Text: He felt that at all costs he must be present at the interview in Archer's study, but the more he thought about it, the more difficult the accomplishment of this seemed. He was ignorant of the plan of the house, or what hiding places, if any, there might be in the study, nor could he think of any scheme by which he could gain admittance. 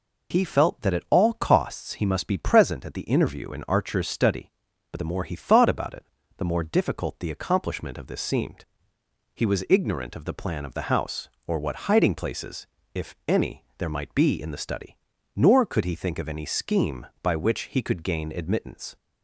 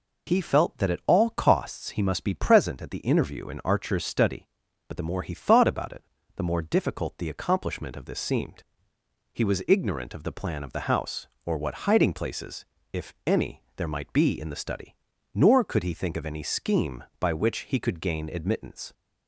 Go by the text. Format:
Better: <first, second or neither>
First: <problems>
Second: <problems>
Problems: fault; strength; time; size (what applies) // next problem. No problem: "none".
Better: neither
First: none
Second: none